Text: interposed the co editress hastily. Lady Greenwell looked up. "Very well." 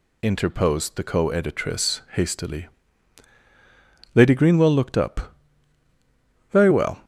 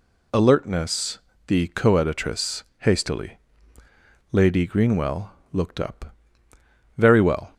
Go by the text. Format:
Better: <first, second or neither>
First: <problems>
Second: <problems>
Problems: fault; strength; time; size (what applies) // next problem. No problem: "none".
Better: first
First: none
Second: says "alertness" for "interposed"; at 0.3 s // pauses between "editress" and "hastily"; slight; at 2.6 s; 0.17 s long // pauses between "Greenwell" and "looked"; slight; at 5.3 s; 0.20 s long